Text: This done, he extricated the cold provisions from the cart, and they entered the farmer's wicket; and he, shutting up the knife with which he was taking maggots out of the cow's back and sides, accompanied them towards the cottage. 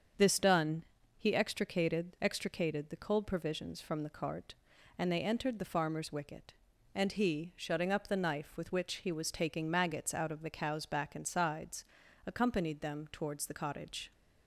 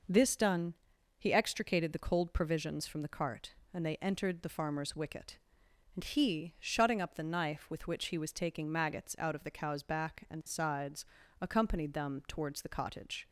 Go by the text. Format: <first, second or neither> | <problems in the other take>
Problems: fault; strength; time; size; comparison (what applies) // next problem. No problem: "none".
second | starts louder than the rest; strong; until 1.5 s; 7 dB // says "extricated" twice; at 2.2 s